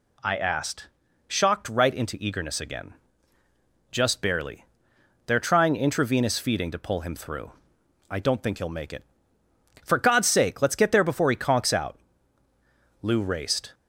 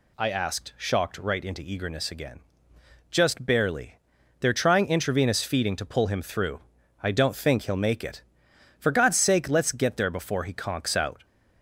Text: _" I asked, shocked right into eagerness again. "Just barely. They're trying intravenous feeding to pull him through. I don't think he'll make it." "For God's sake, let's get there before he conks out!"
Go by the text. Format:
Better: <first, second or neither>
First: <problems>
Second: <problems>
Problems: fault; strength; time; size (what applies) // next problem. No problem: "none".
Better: second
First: goes on to say "Lou raced"; noticeable; from 13.0 s on; 0.72 s long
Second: none